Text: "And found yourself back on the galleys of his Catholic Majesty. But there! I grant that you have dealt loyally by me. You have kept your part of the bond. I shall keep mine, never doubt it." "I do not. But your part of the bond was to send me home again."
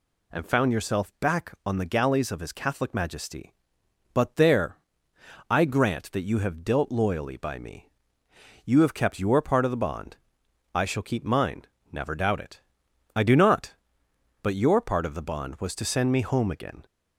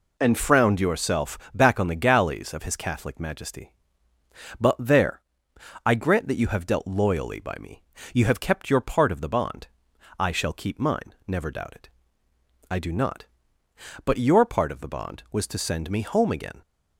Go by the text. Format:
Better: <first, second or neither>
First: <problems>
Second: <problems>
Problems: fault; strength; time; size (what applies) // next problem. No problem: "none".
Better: first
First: none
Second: says "frowned" for "found"; at 0.3 s // pauses between "yourself" and "back"; slight; at 1.3 s; 0.16 s long